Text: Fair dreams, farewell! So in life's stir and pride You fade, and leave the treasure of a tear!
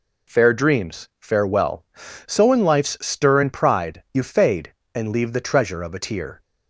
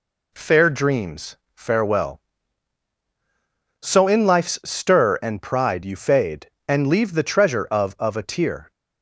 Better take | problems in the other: first | says "of" twice; at 7.9 s

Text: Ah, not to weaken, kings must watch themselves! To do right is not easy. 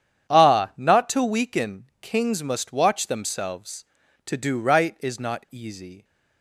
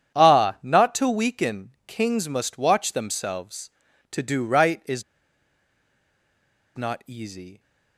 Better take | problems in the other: first | starts louder than the rest; strong; until 1.2 s; 9 dB; strong in the first // pauses between "is" and "not"; strong; at 5.0 s; 1.7 s long

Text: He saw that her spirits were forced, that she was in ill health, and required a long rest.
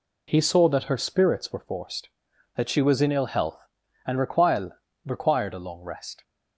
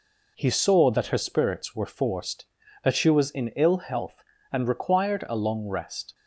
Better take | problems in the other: second | says "required" twice; at 5.0 s

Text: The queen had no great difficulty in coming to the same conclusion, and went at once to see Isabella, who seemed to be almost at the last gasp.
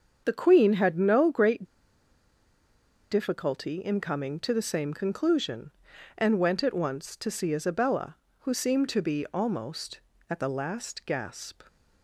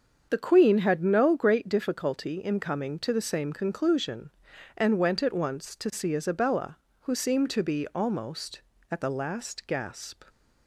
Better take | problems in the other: second | starts louder than the rest; until 1.2 s; 7 dB; also in the second // pauses between "great" and "difficulty"; strong; at 1.6 s; 1.4 s long

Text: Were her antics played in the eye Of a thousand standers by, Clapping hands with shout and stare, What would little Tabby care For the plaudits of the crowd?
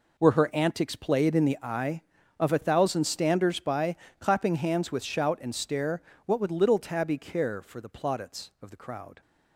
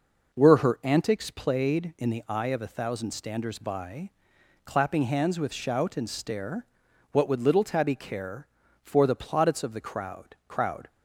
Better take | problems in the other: first | says "crowd" twice; at 10.4 s

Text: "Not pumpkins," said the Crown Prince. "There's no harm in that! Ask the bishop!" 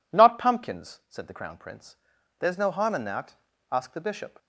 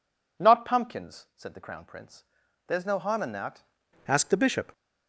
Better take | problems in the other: first | changes voice at "Ask"; from 4.0 s on; 0.7 s long

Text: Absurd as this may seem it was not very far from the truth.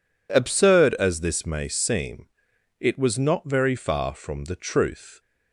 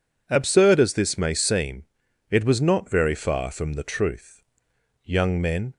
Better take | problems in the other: first | pauses between "seem" and "it"; noticeable; at 1.8 s; 0.46 s long; noticeable in the first // goes on to say "Young men"; noticeable; from 5.0 s on; 0.72 s long

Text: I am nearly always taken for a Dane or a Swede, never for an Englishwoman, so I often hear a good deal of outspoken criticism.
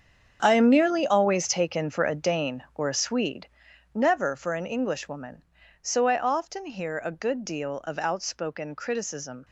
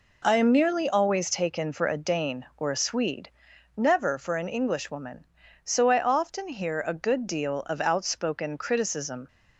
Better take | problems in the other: second | gets quieter; strong; throughout; 12 dB

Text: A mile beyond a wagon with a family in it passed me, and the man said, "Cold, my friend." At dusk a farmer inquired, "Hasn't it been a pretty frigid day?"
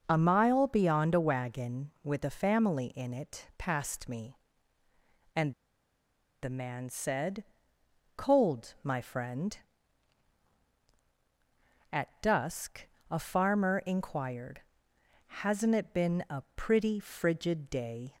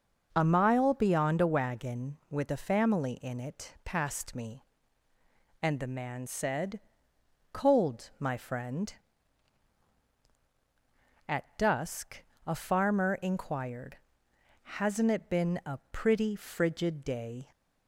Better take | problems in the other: second | pauses between "and" and "the"; noticeable; at 5.5 s; 0.90 s long // pauses between "dusk" and "a"; slight; at 12.8 s; 0.24 s long; slight in the second

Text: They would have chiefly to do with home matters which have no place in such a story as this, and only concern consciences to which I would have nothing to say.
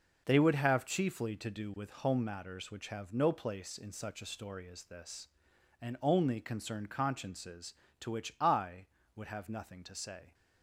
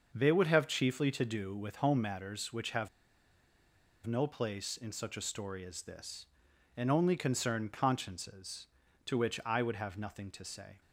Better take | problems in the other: first | starts louder than the rest; until 1.1 s; 6 dB // pauses between "have" and "no"; at 2.8 s; 1.1 s long

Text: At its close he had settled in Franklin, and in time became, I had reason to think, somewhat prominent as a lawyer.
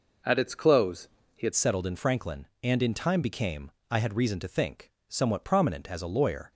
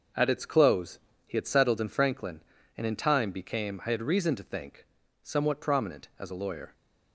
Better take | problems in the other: second | pauses between "close" and "he"; slight; at 1.0 s; 0.26 s long; slight in the second // changes voice at "settled"; from 1.5 s on; 5.0 s long

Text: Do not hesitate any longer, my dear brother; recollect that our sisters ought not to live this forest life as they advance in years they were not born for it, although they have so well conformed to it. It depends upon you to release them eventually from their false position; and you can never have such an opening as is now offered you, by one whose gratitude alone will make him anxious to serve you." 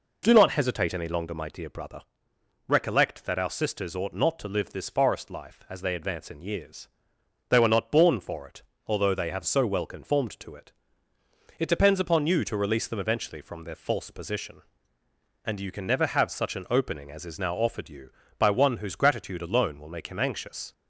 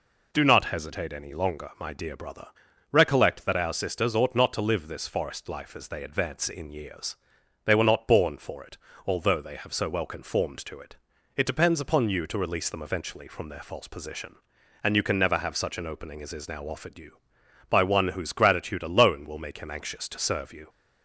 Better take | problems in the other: second | pauses between "years" and "they"; noticeable; at 6.8 s; 0.62 s long; noticeable in the second // stops before "to serve you"; at 20.7 s

